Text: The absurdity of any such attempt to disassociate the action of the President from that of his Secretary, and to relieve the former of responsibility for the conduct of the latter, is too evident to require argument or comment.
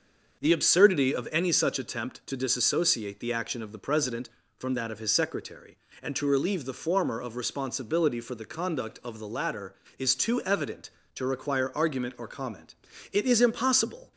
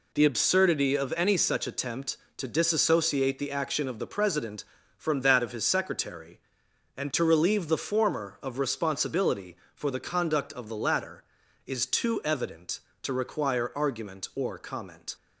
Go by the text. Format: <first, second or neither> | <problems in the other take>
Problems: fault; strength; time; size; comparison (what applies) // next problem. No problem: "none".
second | starts louder than the rest; until 1.4 s; 6.5 dB // goes on to say "It is impossible"; noticeable; from 13.1 s on; 1.0 s long